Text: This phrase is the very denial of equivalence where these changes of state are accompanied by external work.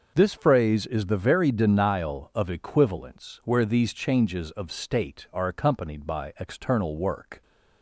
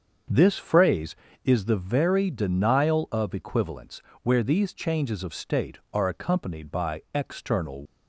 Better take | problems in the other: first | starts louder than the rest; until 1.5 s; 7 dB // pauses between "equivalence" and "where"; slight; at 4.0 s; 0.18 s long // stops before "work"; at 7.8 s

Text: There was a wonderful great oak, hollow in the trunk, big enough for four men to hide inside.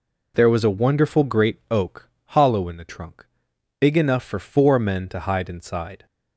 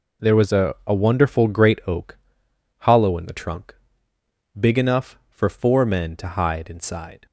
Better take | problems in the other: first | says "a" twice; at 0.8 s

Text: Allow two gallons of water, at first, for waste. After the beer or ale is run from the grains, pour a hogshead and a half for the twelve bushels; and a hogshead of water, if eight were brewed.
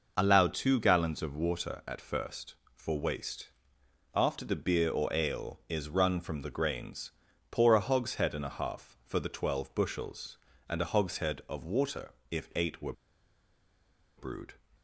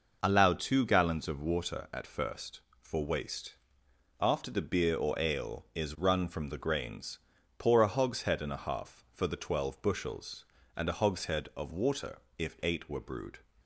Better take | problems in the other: second | pauses between "were" and "brewed"; at 12.9 s; 1.2 s long

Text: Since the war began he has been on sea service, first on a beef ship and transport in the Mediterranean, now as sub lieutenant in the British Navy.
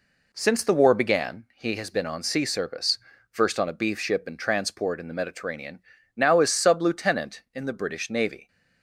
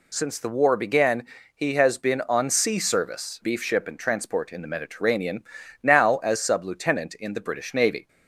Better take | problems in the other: first | pauses between "began" and "he"; slight; at 1.2 s; 0.30 s long // skips "first on a"; at 3.4 s

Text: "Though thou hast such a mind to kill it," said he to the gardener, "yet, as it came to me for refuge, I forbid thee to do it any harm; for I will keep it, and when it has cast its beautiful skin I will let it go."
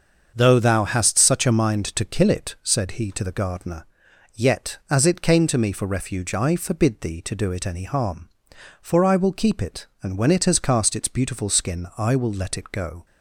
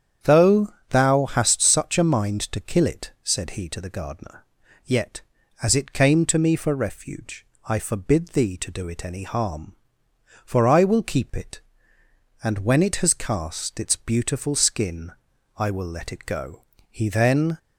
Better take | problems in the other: first | starts louder than the rest; strong; until 1.3 s; 8.5 dB; also in the first // pauses between "Though" and "thou"; slight; at 0.7 s; 0.16 s long // pauses between "skin" and "I"; at 15.1 s; 0.44 s long // goes on to say "He then"; noticeable; from 16.8 s on; 0.70 s long

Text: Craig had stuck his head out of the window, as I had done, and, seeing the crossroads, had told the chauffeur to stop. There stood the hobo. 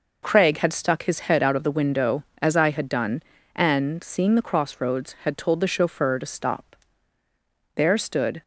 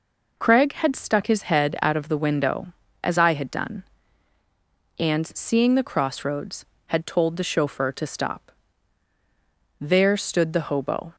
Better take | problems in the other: second | stops before "the hobo"; at 8.4 s

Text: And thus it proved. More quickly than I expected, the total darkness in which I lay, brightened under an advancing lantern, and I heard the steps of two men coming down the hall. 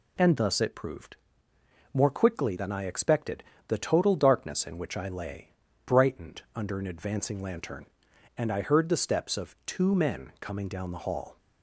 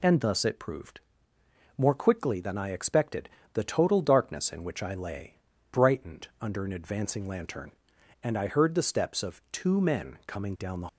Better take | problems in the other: first | stops before "hall"; at 10.8 s

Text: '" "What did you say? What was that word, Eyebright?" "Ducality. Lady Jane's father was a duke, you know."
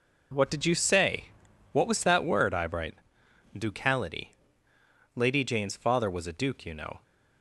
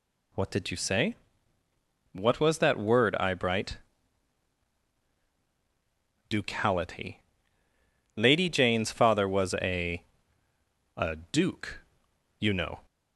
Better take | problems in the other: first | says "a" twice; at 10.9 s

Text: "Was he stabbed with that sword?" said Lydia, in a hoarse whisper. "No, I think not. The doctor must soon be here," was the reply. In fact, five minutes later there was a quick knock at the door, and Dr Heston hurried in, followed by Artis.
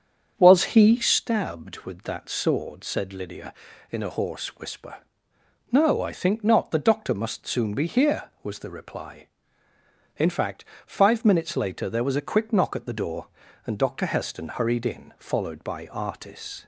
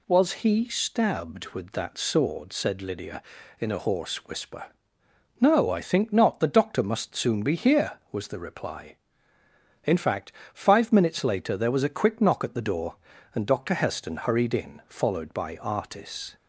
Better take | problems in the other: second | starts louder than the rest; strong; until 1.3 s; 7.5 dB

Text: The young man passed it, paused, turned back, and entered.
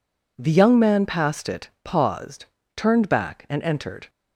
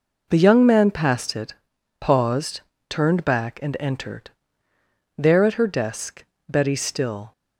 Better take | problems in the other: first | goes on to say "There at her desk Betty still"; strong; from 5.1 s on; 2.1 s long

